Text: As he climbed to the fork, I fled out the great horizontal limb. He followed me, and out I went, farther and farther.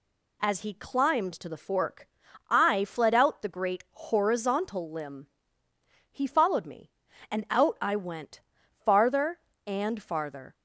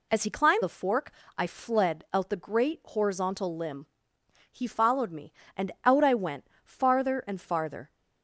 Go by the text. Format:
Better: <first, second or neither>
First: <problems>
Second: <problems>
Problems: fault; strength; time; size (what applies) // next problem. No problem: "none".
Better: first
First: none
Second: skips "to"; at 0.6 s